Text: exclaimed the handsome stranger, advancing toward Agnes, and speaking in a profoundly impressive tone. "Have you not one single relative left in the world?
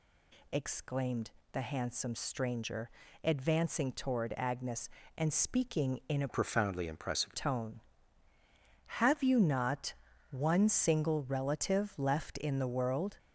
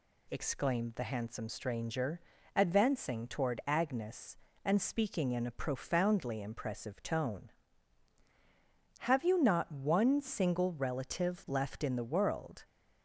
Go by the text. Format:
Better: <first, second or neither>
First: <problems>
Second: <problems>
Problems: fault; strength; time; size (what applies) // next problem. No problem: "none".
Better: second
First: pauses between "exclaimed" and "the"; slight; at 1.2 s; 0.22 s long // changes voice from "profoundly" to "impressive"; from 6.2 to 7.3 s; 1.1 s long // pauses between "not" and "one"; at 9.9 s; 0.38 s long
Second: none